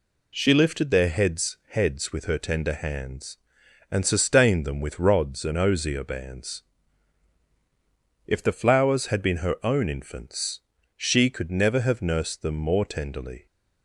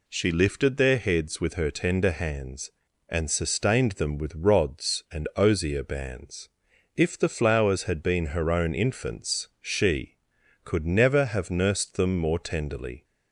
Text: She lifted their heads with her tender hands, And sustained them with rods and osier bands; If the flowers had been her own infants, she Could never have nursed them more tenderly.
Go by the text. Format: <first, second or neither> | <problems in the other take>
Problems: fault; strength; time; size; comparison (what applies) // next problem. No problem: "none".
second | says "heads" twice; at 1.6 s